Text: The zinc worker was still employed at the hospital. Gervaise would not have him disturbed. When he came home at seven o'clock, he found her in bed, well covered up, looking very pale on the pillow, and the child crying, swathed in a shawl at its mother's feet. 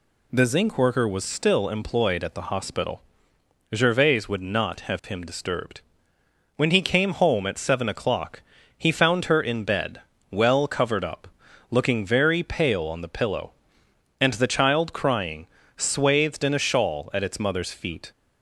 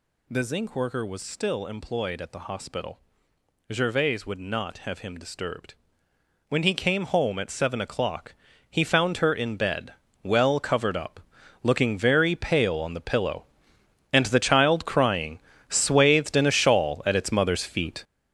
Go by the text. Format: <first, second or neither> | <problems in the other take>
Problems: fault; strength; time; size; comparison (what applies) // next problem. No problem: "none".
first | gets louder; strong; throughout; 10 dB